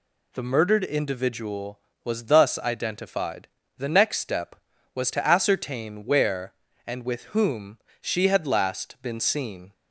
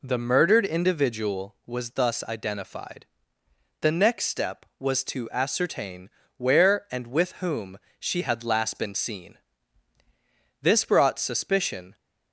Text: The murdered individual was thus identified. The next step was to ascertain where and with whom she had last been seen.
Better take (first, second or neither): first